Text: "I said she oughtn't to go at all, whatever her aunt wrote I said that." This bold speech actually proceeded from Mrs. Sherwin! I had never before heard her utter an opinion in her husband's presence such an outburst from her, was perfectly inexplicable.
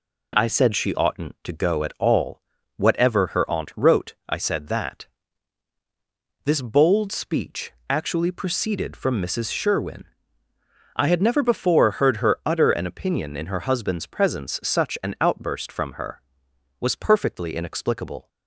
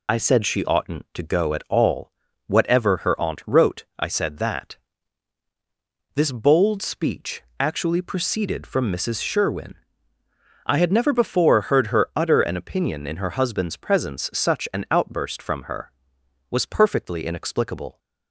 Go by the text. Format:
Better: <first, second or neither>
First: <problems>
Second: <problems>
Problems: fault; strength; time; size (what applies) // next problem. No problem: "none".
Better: first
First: pauses between "speech" and "actually"; slight; at 7.7 s; 0.16 s long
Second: loses the start of "I"; at 0.0 s; 60 ms // pauses between "speech" and "actually"; slight; at 7.4 s; 0.16 s long